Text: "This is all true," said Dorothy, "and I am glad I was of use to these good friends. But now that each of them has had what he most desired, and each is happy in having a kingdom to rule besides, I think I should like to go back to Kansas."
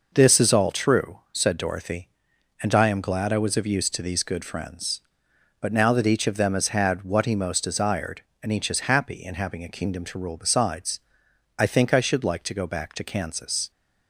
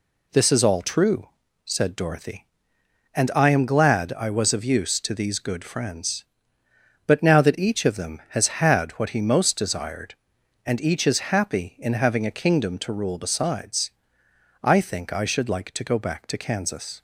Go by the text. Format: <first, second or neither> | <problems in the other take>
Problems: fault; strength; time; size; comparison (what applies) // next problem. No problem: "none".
neither | none